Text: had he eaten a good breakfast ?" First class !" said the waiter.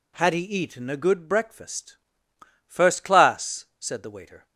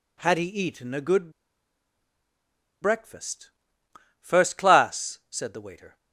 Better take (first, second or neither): first